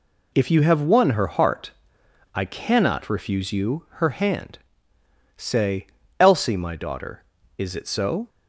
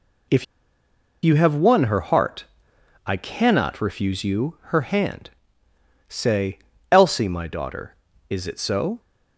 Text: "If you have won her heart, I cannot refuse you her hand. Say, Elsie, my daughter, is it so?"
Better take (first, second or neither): first